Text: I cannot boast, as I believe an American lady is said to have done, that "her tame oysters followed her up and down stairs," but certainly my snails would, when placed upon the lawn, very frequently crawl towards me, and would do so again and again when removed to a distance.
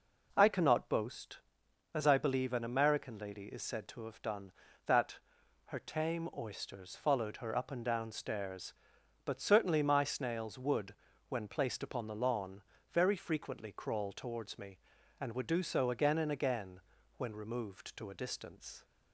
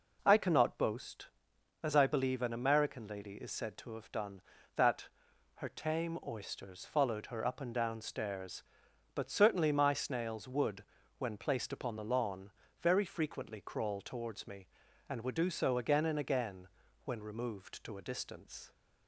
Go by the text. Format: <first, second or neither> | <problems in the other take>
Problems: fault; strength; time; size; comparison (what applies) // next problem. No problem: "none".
neither | pauses between "that" and "her"; noticeable; the same in both // pauses between "again" and "when"; the same in both